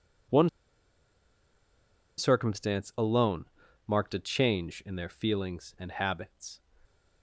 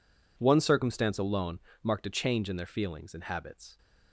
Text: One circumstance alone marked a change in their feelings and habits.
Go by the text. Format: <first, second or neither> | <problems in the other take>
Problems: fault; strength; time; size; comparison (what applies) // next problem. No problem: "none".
second | pauses between "One" and "circumstance"; strong; at 0.4 s; 1.6 s long // pauses between "alone" and "marked"; at 3.4 s; 0.40 s long; slight in the second